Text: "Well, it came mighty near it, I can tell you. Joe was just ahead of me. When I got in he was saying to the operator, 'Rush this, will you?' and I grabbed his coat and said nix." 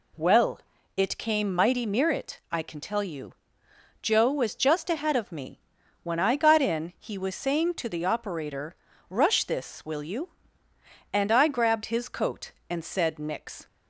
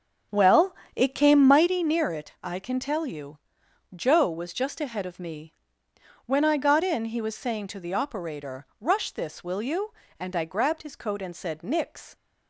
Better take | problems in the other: first | starts louder than the rest; until 1.8 s; 6.5 dB

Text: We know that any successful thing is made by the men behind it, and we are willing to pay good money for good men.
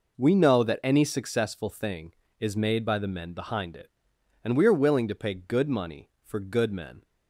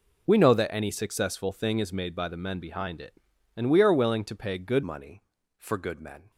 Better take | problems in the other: first | changes voice at "money"; from 4.8 s on; 1.5 s long

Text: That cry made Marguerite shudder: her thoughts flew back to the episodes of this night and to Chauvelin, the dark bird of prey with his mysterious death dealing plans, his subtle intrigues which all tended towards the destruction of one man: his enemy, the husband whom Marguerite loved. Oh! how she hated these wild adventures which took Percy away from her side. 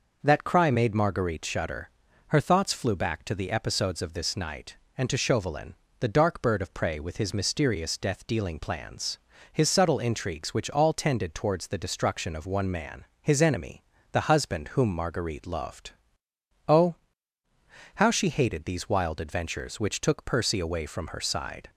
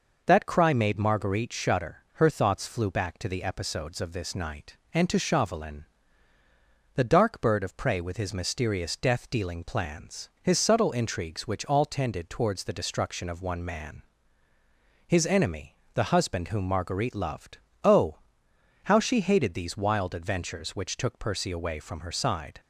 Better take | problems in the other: neither | none

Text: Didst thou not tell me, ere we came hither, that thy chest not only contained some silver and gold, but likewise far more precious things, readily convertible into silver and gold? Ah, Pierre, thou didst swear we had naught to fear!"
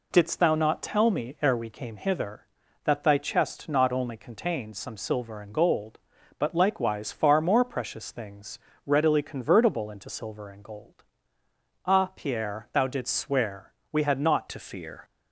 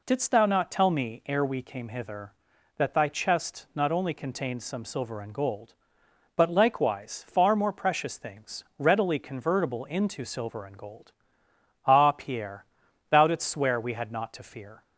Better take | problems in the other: second | pauses between "swear" and "we"; slight; at 13.7 s; 0.20 s long // changes voice at "to"; from 14.4 s on; 0.6 s long

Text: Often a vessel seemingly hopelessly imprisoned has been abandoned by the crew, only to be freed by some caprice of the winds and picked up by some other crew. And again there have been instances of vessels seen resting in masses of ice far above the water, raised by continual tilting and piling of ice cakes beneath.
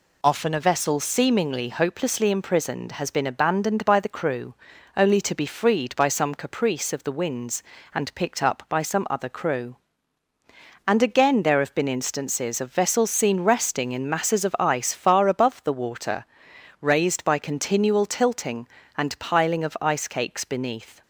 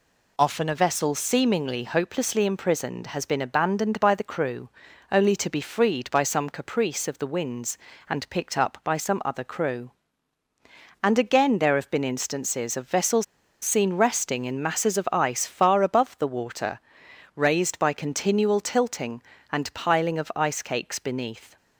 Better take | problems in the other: first | pauses between "vessels" and "seen"; at 13.2 s; 0.37 s long

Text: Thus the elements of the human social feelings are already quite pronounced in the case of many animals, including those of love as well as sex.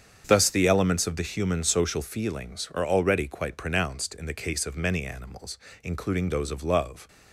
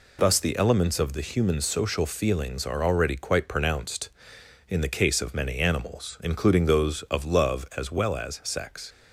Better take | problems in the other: second | starts louder than the rest; strong; until 1.2 s; 7.5 dB // stops before "as well as sex"; at 7.0 s

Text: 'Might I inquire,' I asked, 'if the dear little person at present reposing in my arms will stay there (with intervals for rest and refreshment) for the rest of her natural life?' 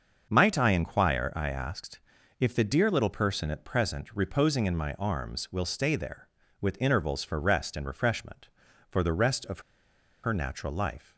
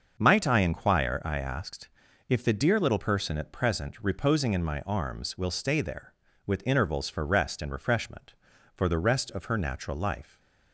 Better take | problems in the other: second | starts louder than the rest; until 1.3 s; 6.5 dB; also in the second // pauses between "of" and "her"; noticeable; at 9.5 s; 0.63 s long

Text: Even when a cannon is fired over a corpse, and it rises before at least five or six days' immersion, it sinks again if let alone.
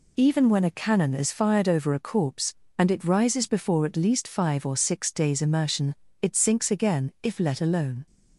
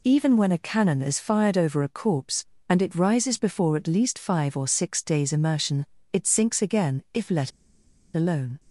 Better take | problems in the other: first | pauses between "let" and "alone"; noticeable; at 7.5 s; 0.63 s long

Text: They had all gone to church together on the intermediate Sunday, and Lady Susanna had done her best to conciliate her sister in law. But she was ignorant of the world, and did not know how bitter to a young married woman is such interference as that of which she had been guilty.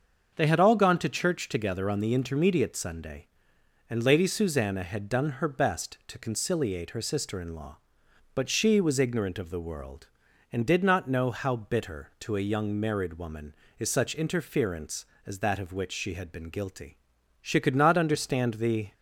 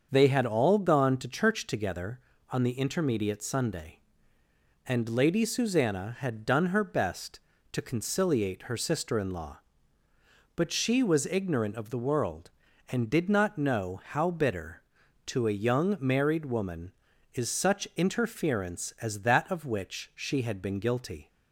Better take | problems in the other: second | starts louder than the rest; until 1.3 s; 6.5 dB; also in the second // goes on to say "She could not understand the"; from 17.4 s on; 1.5 s long

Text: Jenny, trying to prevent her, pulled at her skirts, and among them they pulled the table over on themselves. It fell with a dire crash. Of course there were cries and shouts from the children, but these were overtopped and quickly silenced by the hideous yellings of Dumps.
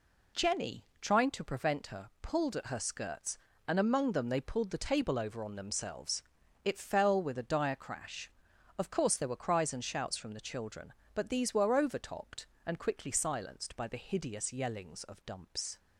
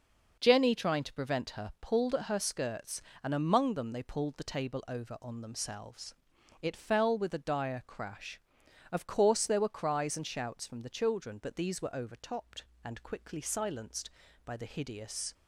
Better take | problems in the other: first | stops before "yellings of Dumps"; at 15.3 s

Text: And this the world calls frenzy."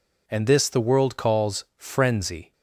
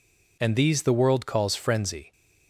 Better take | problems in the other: first | says "these" for "this"; at 0.5 s

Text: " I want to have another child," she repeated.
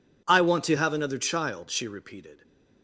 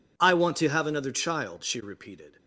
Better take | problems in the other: neither | none

